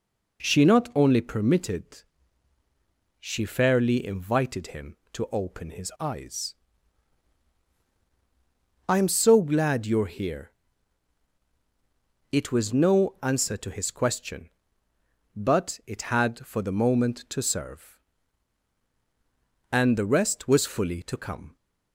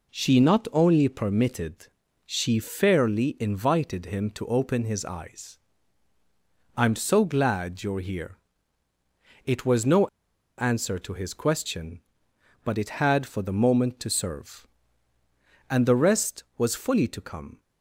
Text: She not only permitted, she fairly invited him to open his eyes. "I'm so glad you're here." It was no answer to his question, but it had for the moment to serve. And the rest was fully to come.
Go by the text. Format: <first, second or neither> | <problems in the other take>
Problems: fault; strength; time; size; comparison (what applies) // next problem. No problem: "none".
first | pauses between "no" and "answer"; noticeable; at 10.0 s; 0.50 s long